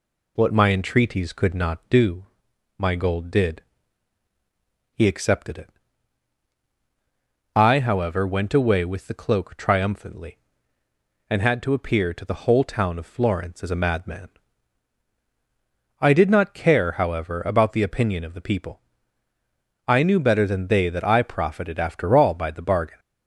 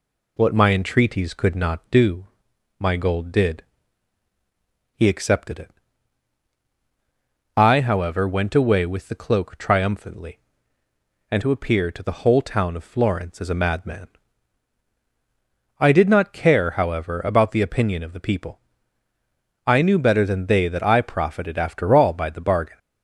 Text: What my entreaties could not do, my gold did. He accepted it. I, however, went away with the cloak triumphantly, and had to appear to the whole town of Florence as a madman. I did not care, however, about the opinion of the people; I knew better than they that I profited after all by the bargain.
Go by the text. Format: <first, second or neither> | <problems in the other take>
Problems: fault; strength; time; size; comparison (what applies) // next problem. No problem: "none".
first | skips "had"; at 11.4 s